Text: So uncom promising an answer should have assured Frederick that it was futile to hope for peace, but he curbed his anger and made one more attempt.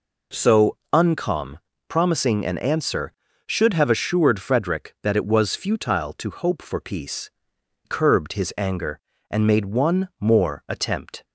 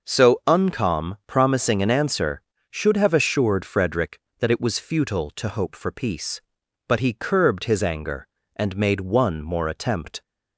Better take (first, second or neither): second